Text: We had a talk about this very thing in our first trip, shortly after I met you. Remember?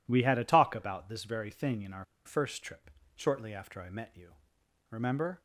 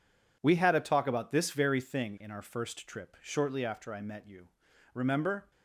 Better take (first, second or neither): second